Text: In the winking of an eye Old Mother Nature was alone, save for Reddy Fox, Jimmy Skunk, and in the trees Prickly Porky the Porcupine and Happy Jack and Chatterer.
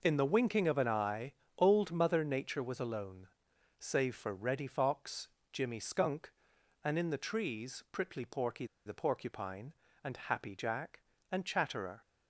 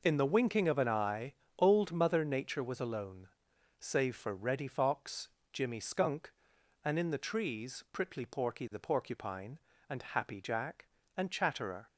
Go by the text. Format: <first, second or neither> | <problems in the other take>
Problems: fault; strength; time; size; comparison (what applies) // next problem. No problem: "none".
second | pauses between "eye" and "Old"; slight; at 1.3 s; 0.24 s long; slight in the second // pauses between "Porky" and "the"; slight; at 8.6 s; 0.21 s long